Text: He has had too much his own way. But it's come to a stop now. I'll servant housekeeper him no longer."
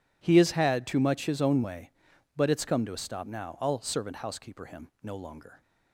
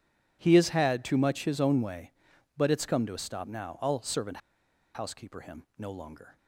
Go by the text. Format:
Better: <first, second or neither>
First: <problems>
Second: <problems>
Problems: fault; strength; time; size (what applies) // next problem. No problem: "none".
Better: first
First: none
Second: pauses between "servant" and "housekeeper"; noticeable; at 4.3 s; 0.56 s long